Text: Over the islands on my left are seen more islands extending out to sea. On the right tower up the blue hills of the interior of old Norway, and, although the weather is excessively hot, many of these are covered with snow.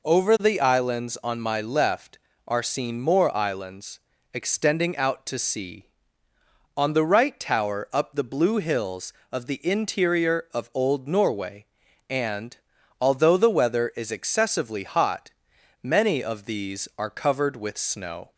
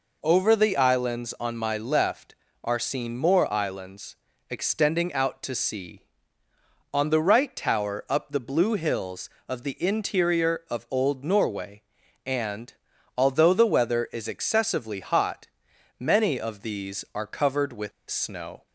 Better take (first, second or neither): first